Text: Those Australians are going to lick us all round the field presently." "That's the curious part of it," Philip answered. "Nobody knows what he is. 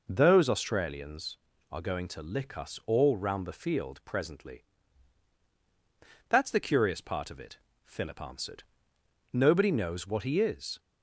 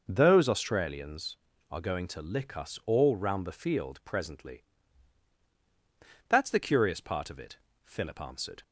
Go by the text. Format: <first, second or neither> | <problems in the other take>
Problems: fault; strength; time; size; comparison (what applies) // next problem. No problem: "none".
first | stops before "Nobody knows what he is"; at 8.6 s